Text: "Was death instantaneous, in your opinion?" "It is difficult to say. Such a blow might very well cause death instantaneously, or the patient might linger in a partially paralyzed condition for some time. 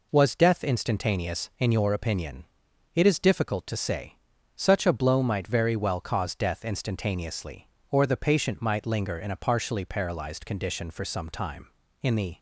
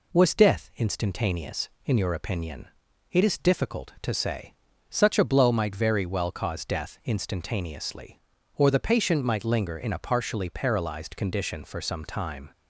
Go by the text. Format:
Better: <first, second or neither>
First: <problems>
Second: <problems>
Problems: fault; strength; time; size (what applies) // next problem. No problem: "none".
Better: second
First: goes on to say "In the"; slight; from 12.0 s on; 0.38 s long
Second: none